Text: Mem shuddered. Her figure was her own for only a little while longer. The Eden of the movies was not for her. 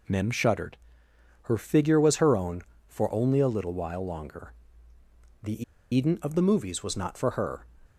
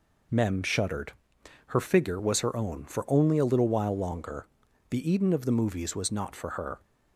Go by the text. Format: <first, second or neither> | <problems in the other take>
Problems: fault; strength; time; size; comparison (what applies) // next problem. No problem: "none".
second | pauses between "The" and "Eden"; slight; at 5.6 s; 0.30 s long